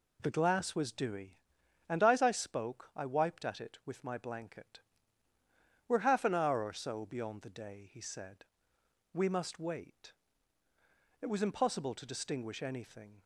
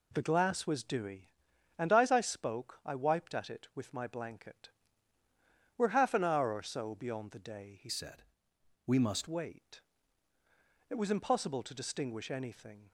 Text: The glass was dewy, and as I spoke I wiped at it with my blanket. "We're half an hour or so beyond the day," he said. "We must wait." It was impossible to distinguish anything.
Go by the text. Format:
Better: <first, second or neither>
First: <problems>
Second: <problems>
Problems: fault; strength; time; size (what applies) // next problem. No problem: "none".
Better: first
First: none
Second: changes voice from "said" to "must"; from 7.8 to 9.2 s; 1.4 s long